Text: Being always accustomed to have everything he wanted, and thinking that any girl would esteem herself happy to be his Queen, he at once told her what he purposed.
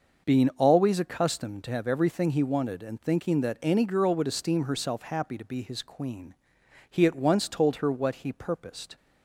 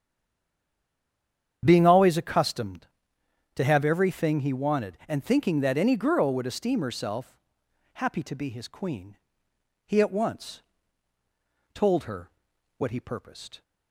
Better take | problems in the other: first | stays silent before the first word; noticeable; until 1.6 s; 1.6 s long // starts louder than the rest; strong; until 2.6 s; 8.5 dB; noticeable in the first // pauses between "herself" and "happy"; noticeable; at 7.3 s; 0.56 s long // pauses between "once" and "told"; at 10.5 s; 1.1 s long // pauses between "her" and "what"; noticeable; at 12.2 s; 0.48 s long

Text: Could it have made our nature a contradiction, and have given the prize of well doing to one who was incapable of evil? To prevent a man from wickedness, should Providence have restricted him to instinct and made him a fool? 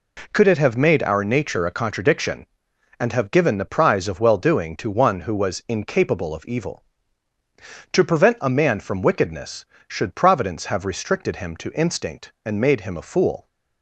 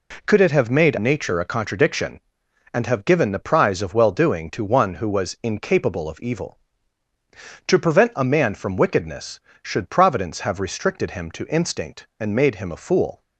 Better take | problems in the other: first | skips "our"; at 0.9 s

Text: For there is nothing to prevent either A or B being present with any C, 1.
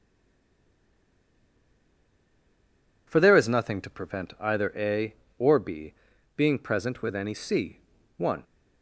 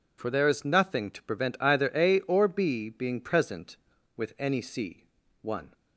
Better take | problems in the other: second | stays silent before the first word; strong; until 3.0 s; 3.0 s long // pauses between "B" and "being"; at 5.9 s; 0.42 s long

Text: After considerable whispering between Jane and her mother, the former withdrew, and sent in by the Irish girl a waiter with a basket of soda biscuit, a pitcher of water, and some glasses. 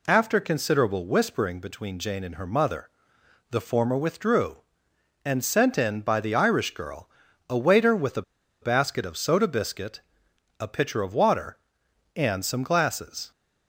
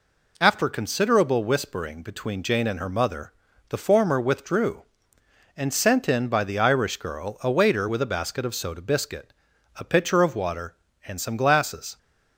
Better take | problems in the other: second | pauses between "girl" and "a"; at 7.0 s; 0.40 s long // pauses between "a" and "basket"; at 8.2 s; 0.40 s long

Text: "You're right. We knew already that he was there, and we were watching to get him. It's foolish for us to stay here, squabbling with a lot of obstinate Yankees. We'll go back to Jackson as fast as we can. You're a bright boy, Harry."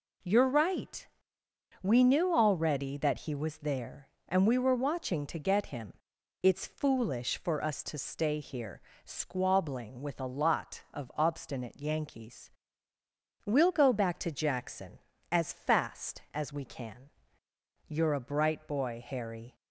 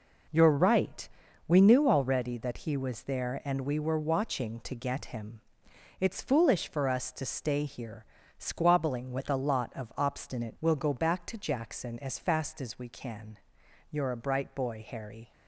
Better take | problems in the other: first | skips "Yankees"; at 10.5 s

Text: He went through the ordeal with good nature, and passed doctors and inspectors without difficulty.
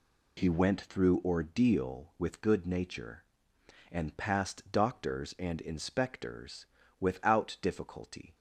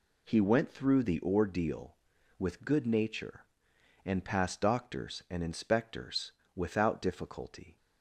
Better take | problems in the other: second | skips "the"; at 1.2 s // pauses between "inspectors" and "without"; slight; at 6.6 s; 0.34 s long; slight in the second

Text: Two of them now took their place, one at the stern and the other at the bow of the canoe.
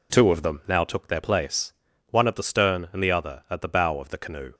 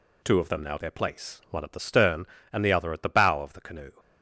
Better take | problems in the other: first | skips "took"; at 0.7 s

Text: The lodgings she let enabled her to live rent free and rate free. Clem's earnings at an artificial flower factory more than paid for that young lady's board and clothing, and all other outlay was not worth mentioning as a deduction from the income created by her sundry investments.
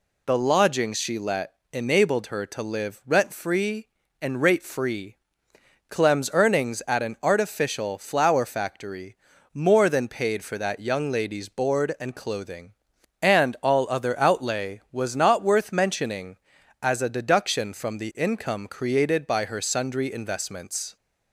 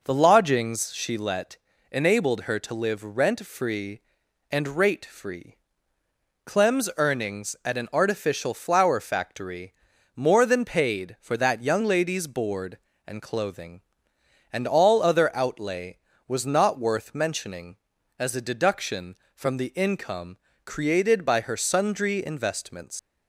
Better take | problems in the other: first | pauses between "let" and "enabled"; slight; at 1.5 s; 0.34 s long; slight in the first // pauses between "factory" and "more"; at 9.7 s; 0.44 s long; slight in the first // pauses between "income" and "created"; slight; at 20.3 s; 0.26 s long // leaves "investments" unfinished; at 22.9 s; 120 ms

